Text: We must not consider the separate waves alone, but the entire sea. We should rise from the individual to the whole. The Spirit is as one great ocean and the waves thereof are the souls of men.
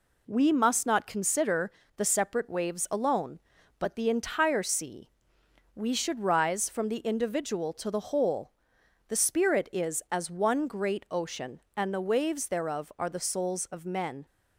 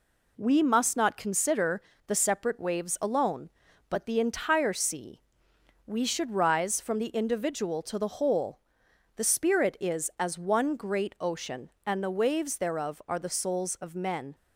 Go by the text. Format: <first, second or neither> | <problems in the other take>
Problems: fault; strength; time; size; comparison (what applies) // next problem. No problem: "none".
neither | pauses between "consider" and "the"; slight; the same in both